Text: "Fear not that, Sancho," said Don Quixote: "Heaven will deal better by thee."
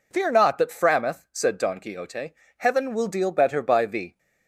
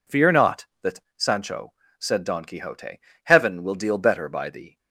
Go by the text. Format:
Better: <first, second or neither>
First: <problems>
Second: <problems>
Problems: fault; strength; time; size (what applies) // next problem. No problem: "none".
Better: second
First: says "Frameth" for "Sancho"; at 0.6 s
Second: none